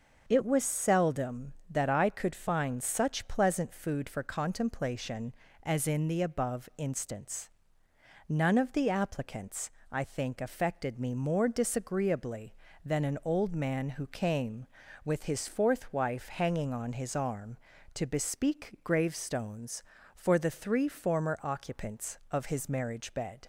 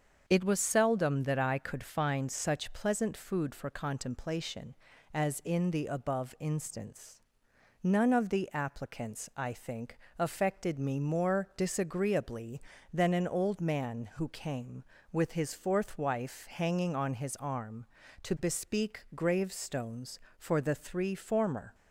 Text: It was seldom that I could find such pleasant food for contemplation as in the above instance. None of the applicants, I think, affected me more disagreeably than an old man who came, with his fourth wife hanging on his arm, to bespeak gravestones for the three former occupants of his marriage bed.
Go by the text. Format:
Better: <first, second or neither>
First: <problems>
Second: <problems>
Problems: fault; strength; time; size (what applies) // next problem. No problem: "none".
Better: first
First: starts louder than the rest; until 1.3 s; 6.5 dB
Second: starts louder than the rest; until 1.2 s; 7 dB // stops before "occupants of his marriage bed"; at 21.7 s